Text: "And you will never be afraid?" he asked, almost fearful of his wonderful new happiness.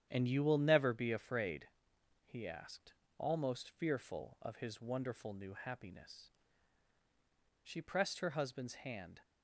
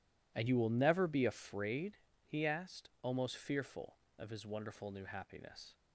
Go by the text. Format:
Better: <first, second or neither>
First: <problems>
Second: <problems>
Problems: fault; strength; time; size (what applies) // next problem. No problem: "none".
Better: second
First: starts louder than the rest; strong; until 1.1 s; 9.5 dB // goes on to say "She pressed her husband's hand"; from 7.6 s on; 1.5 s long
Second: none